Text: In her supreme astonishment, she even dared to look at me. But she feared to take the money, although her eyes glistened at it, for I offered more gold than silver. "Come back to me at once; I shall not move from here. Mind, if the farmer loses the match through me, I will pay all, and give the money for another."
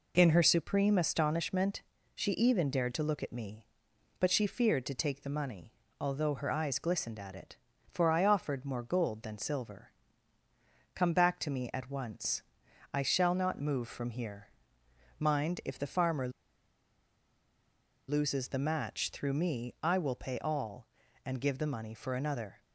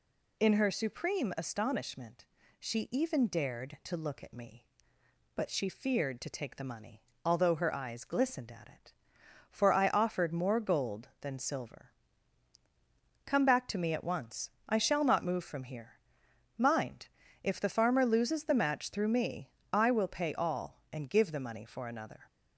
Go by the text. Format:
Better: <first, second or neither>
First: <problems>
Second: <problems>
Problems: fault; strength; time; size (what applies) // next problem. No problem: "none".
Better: second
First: pauses between "farmer" and "loses"; strong; at 16.2 s; 1.7 s long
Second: none